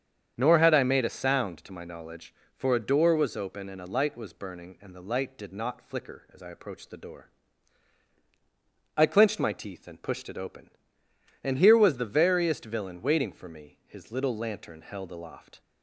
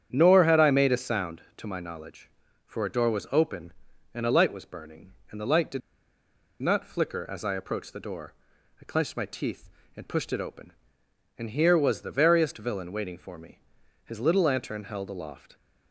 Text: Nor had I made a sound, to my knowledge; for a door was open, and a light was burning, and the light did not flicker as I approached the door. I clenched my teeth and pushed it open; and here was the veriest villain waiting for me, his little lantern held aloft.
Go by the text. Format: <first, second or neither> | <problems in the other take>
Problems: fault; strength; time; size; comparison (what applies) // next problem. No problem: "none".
first | starts louder than the rest; strong; until 1.1 s; 9 dB; strong in the first // pauses between "did" and "not"; noticeable; at 5.8 s; 0.80 s long